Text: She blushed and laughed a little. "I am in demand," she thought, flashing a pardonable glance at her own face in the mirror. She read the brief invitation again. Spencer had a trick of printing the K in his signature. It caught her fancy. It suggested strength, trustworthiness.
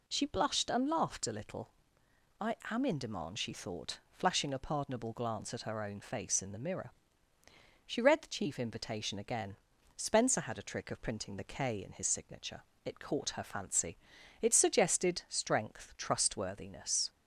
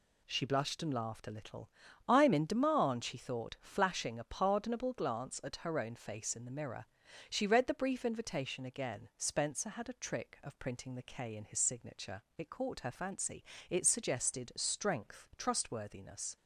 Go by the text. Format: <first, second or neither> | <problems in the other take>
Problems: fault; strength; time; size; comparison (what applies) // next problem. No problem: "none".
second | pauses between "I" and "am"; slight; at 2.5 s; 0.16 s long // says "chief" for "brief"; at 8.2 s